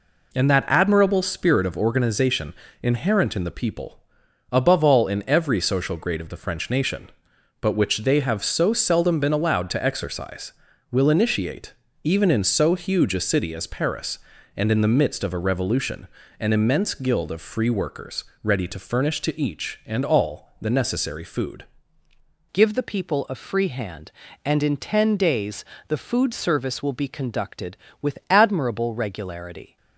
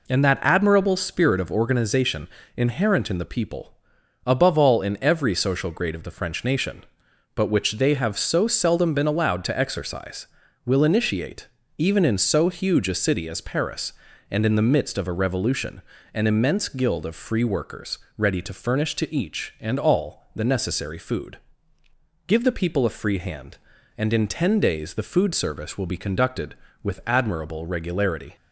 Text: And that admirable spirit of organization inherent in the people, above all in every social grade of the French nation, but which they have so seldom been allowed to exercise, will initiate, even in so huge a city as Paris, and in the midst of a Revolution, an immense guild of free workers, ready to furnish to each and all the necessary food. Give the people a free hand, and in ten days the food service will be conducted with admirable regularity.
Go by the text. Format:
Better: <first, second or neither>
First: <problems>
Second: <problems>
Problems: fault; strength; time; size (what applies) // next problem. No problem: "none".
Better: second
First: pauses between "organization" and "inherent"; slight; at 2.5 s; 0.28 s long // changes voice at "Give"; from 22.5 s on; 7.2 s long // pauses between "days" and "the"; slight; at 25.6 s; 0.22 s long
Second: pauses between "organization" and "inherent"; slight; at 2.2 s; 0.28 s long